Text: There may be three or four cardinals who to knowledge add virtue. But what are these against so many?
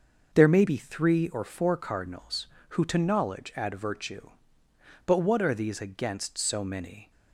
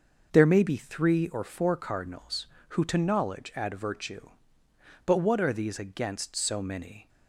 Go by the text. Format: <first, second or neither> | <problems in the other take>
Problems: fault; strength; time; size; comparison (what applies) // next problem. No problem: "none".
neither | none